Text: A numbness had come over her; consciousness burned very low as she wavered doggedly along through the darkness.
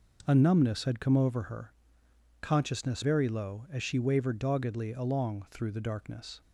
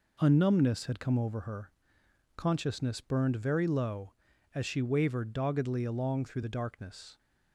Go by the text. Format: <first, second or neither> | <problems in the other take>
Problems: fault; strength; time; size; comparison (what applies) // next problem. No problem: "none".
second | skips "burned"; at 3.0 s